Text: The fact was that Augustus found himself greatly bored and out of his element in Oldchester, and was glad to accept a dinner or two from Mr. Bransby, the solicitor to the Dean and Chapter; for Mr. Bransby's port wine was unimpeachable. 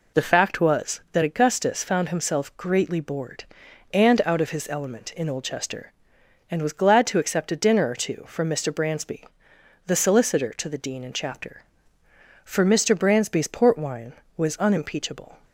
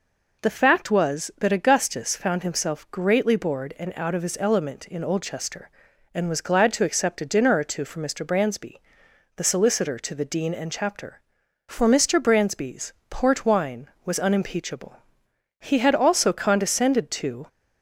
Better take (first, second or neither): first